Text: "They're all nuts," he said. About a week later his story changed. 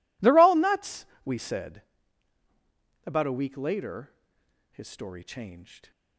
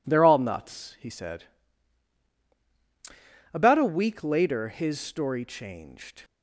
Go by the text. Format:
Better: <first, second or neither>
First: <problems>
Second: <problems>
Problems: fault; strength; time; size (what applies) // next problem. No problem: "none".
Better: second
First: says "we" for "he"; at 1.2 s // pauses between "later" and "his"; noticeable; at 4.1 s; 0.60 s long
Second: none